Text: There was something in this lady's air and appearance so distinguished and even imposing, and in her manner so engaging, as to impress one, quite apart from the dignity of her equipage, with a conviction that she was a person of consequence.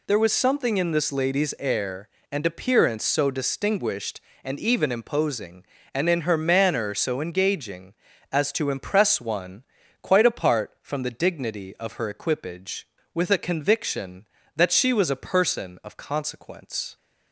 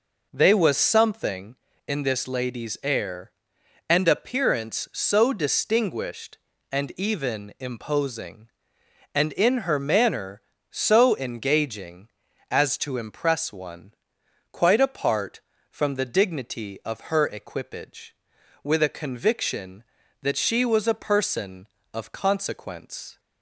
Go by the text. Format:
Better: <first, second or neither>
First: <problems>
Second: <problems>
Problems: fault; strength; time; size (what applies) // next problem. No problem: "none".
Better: first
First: none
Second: says "They" for "There"; at 0.3 s